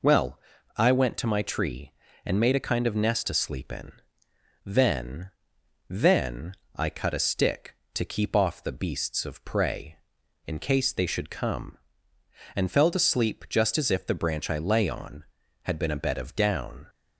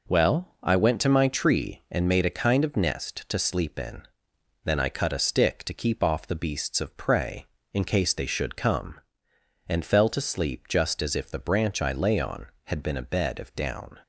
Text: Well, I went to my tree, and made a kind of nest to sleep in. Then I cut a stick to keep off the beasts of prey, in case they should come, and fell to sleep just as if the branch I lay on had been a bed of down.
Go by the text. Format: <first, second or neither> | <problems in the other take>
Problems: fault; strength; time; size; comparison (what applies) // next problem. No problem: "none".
second | says "Then" twice; at 5.9 s